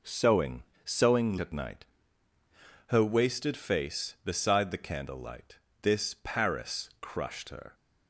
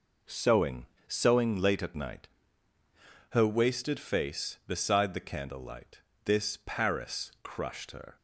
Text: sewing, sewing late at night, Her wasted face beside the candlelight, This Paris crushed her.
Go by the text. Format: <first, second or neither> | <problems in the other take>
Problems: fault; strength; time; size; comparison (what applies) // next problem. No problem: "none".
second | skips "late"; at 1.3 s